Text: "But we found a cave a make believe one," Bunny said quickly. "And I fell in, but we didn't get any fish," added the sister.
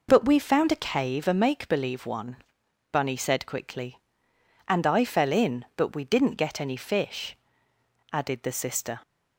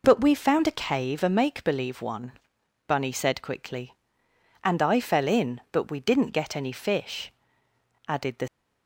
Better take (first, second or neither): first